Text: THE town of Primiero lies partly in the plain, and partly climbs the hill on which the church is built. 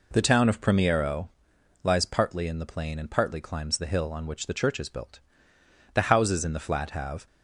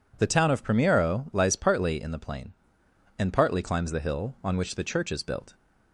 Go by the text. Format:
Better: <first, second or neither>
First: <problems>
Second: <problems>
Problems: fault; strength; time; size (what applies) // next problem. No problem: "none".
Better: second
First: pauses between "Primiero" and "lies"; noticeable; at 1.2 s; 0.54 s long // goes on to say "The houses in the flat have"; from 5.9 s on; 1.3 s long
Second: none